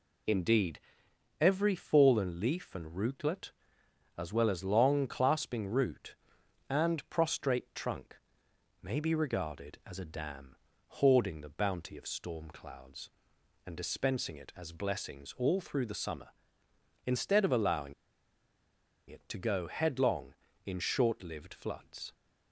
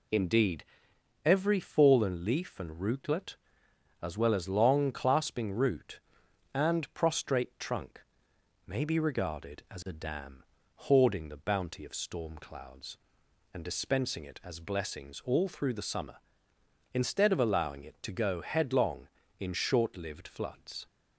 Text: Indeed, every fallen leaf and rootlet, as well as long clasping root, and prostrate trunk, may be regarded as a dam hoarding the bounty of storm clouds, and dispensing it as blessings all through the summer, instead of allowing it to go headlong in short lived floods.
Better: second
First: pauses between "dam" and "hoarding"; at 10.5 s; 0.44 s long // pauses between "allowing" and "it"; at 17.9 s; 1.1 s long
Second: pauses between "dam" and "hoarding"; at 10.4 s; 0.44 s long

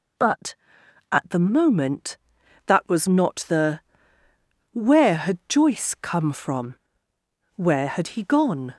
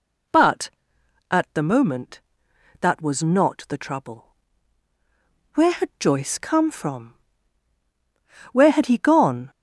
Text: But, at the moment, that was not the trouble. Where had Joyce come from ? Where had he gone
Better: second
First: skips "trouble"; at 4.2 s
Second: none

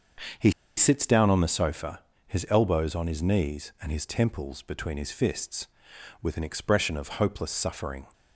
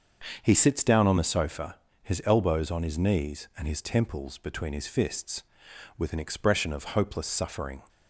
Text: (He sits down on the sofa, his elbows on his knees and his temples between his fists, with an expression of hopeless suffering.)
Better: second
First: starts louder than the rest; until 1.6 s; 6.5 dB // pauses between "He" and "sits"; slight; at 0.5 s; 0.26 s long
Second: starts louder than the rest; until 1.4 s; 6.5 dB

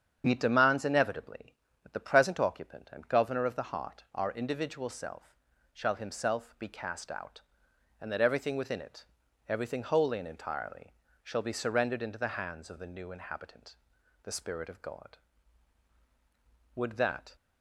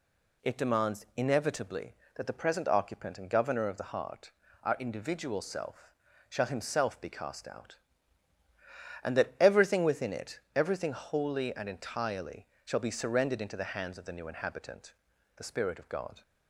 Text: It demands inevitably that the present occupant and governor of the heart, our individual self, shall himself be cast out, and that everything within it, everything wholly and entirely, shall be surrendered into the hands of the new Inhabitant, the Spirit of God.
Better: second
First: starts louder than the rest; strong; until 1.3 s; 8 dB // goes on to say "Would that"; from 16.7 s on; 0.60 s long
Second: none

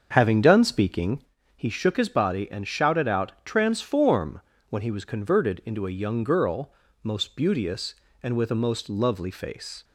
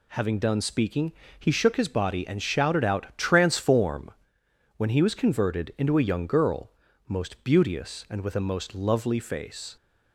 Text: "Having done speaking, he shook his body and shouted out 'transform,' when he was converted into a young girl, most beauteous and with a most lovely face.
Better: second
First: starts louder than the rest; until 1.4 s; 7 dB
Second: none

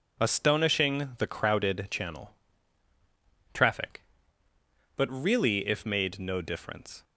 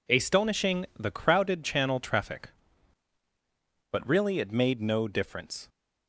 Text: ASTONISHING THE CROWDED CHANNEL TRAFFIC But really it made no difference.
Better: second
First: pauses between "CHANNEL" and "TRAFFIC"; at 2.3 s; 1.1 s long // says "if" for "it"; at 5.6 s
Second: none

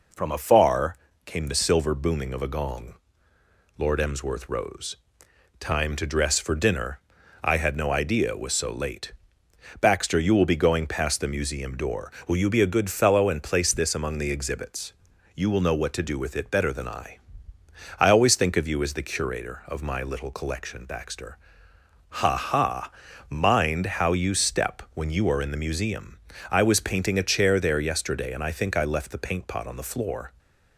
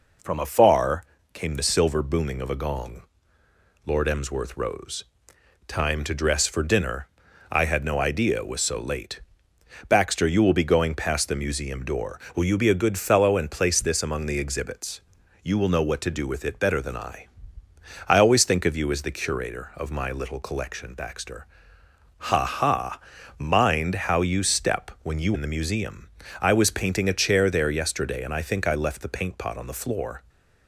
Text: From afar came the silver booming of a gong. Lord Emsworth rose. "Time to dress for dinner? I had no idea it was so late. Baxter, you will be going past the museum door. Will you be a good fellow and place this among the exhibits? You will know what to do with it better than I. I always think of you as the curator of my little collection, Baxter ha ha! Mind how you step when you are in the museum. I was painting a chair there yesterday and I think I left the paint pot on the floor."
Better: first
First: pauses between "afar" and "came"; slight; at 0.9 s; 0.28 s long // pauses between "Baxter" and "ha"; noticeable; at 21.3 s; 0.78 s long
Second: pauses between "afar" and "came"; slight; at 1.0 s; 0.28 s long // pauses between "Baxter" and "ha"; noticeable; at 21.4 s; 0.78 s long // skips "are"; at 25.3 s

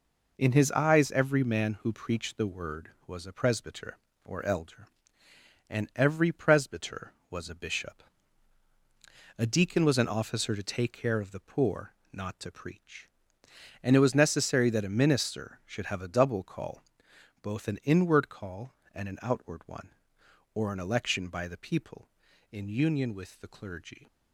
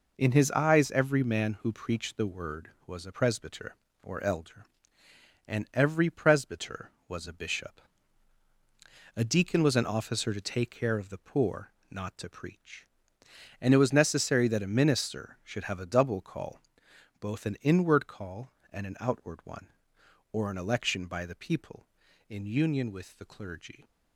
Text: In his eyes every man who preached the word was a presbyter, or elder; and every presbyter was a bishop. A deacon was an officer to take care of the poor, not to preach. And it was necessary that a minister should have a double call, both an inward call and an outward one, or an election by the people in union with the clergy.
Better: neither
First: none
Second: none

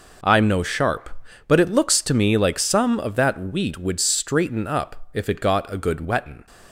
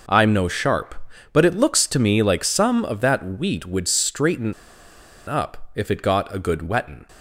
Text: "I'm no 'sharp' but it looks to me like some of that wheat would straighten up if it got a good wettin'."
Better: first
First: none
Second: pauses between "straighten" and "up"; noticeable; at 4.5 s; 0.74 s long

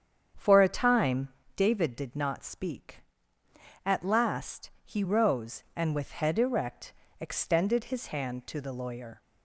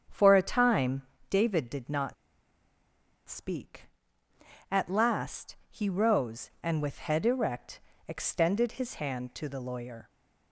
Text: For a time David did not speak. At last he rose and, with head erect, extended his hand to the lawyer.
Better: first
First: starts louder than the rest; strong; until 1.6 s; 8 dB // pauses between "time" and "David"; slight; at 1.2 s; 0.26 s long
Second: starts louder than the rest; strong; until 1.3 s; 8 dB // pauses between "time" and "David"; slight; at 1.0 s; 0.26 s long // pauses between "not" and "speak"; at 2.1 s; 1.1 s long

